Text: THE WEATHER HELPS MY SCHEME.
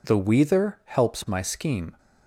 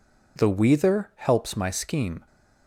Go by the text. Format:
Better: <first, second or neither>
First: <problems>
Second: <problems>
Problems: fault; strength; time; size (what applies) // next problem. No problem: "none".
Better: neither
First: none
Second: none